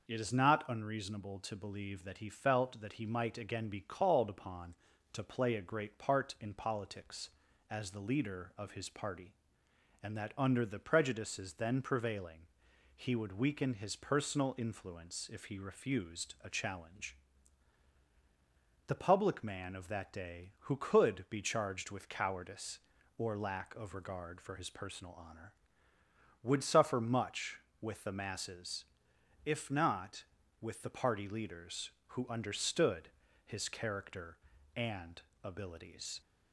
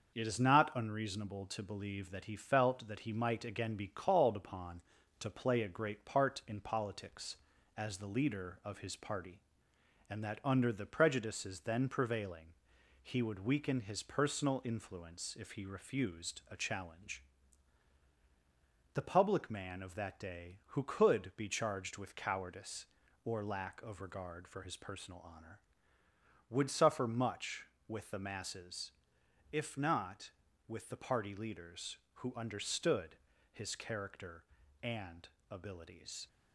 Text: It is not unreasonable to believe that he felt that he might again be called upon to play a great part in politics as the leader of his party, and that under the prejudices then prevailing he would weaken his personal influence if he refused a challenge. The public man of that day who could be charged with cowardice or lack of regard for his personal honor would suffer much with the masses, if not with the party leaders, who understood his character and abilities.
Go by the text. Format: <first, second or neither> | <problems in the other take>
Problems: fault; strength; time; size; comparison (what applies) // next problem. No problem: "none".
first | gets quieter; throughout; 3.5 dB // pauses between "prevailing" and "he"; noticeable; at 12.4 s; 0.54 s long; noticeable in the first // pauses between "understood" and "his"; slight; at 33.1 s; 0.34 s long; slight in the first // pauses between "and" and "abilities"; slight; at 35.2 s; 0.24 s long; slight in the first